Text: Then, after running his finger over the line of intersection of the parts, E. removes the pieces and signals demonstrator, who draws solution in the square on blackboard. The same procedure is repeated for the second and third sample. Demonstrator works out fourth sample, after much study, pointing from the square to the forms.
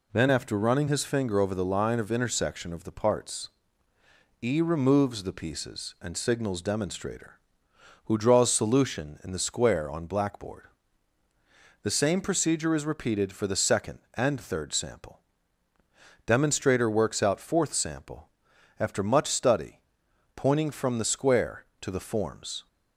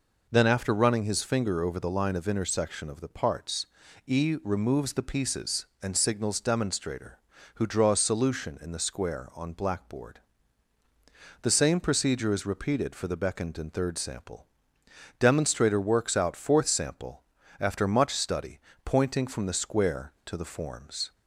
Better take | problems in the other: first | says "beckoned" for "second"; at 13.1 s

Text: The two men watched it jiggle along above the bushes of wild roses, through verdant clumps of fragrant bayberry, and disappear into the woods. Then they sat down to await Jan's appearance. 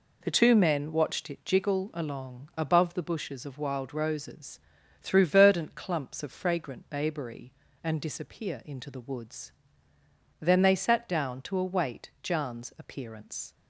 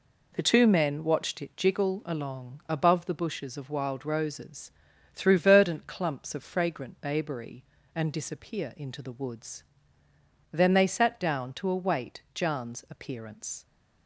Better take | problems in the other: neither | none

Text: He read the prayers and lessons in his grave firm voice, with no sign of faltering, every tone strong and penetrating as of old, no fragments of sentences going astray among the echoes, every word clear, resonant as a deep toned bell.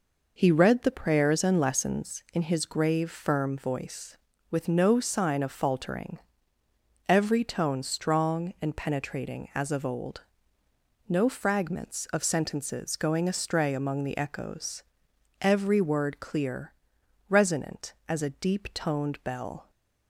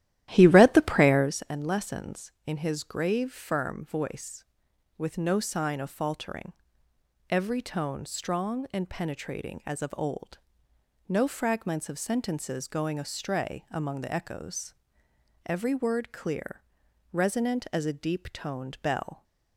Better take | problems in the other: first | starts louder than the rest; strong; until 1.4 s; 13 dB

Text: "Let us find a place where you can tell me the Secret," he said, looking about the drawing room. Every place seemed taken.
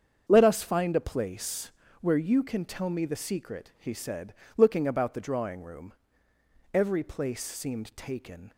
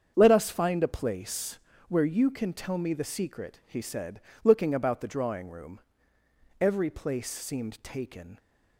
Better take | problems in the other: neither | starts louder than the rest; strong; the same in both // pauses between "place" and "where"; slight; the same in both

